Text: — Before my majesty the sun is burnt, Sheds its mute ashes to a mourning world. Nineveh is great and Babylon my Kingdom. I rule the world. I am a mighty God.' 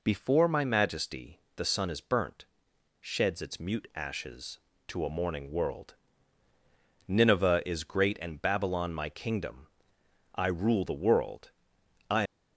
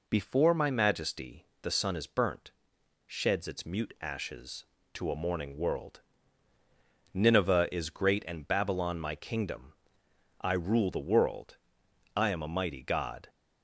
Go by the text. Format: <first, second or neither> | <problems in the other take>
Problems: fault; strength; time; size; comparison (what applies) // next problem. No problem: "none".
second | pauses between "majesty" and "the"; slight; at 1.4 s; 0.16 s long; slight in the second // stops before "am a mighty God"; at 12.2 s